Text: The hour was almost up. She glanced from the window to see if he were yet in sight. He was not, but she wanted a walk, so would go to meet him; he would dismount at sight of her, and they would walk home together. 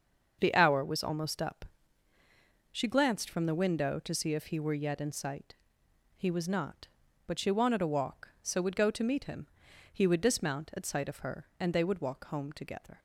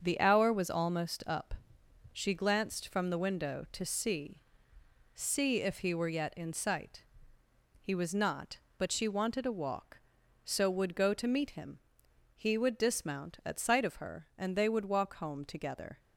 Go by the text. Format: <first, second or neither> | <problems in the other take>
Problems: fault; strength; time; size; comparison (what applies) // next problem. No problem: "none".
first | starts louder than the rest; until 1.0 s; 6.5 dB; also in the first // says "see" twice; at 5.1 s